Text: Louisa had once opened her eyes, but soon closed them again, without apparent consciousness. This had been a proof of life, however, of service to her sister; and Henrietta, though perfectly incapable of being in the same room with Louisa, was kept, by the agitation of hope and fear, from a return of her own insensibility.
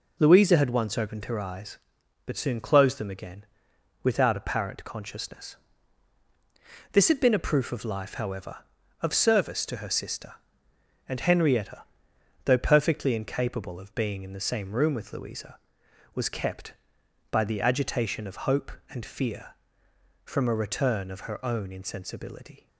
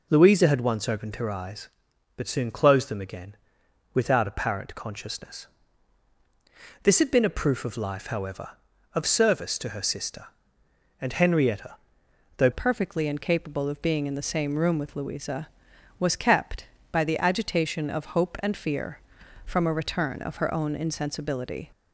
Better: first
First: none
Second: changes voice at "perfectly"; from 12.5 s on; 9.2 s long

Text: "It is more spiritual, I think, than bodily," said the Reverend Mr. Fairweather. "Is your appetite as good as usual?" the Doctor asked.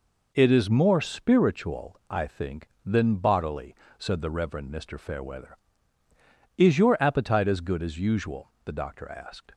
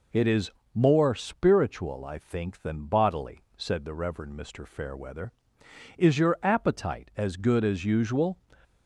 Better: first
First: none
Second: pauses between "is" and "more"; slight; at 0.5 s; 0.22 s long // stops before "the Doctor asked"; at 8.6 s

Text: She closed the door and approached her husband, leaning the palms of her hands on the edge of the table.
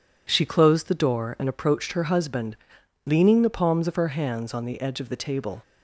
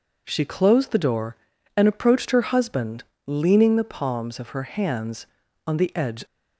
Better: first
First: none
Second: stops before "of the table"; at 6.2 s

